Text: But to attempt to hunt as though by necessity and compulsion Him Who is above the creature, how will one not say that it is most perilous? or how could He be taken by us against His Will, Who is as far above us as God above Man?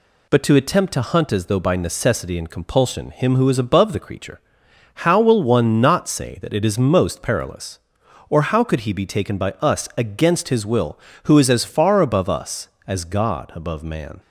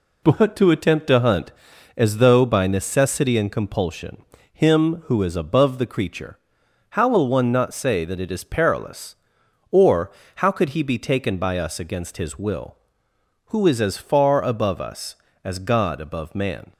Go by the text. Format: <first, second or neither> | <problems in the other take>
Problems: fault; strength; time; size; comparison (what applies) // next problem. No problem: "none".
first | pauses between "compulsion" and "Him"; slight; at 4.2 s; 0.28 s long // skips "most"; at 8.4 s // pauses between "or" and "how"; slight; at 10.0 s; 0.26 s long